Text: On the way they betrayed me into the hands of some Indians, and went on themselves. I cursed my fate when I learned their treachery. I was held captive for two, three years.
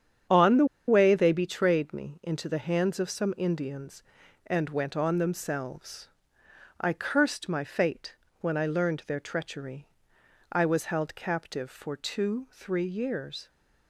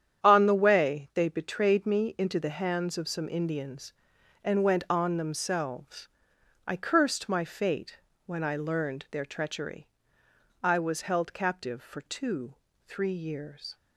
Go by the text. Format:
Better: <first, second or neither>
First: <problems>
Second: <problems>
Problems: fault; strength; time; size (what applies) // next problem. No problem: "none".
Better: second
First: starts louder than the rest; strong; until 1.5 s; 8.5 dB // pauses between "the" and "way"; slight; at 0.6 s; 0.21 s long // pauses between "fate" and "when"; slight; at 8.1 s; 0.26 s long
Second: starts louder than the rest; strong; until 1.2 s; 9 dB // pauses between "fate" and "when"; slight; at 7.9 s; 0.30 s long